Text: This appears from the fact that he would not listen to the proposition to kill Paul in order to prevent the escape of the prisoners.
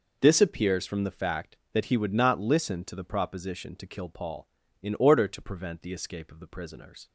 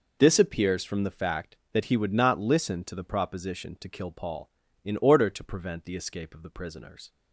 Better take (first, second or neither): neither